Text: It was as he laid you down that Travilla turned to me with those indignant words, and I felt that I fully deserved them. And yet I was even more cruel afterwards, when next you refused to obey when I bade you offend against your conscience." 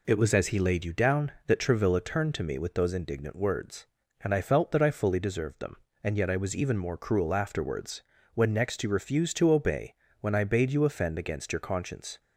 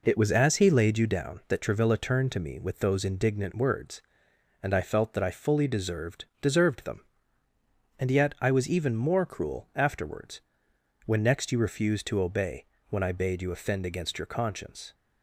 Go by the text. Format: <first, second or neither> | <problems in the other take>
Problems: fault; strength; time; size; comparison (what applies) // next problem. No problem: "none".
first | says "deserved" twice; at 6.4 s // pauses between "obey" and "when"; slight; at 12.6 s; 0.24 s long; slight in the first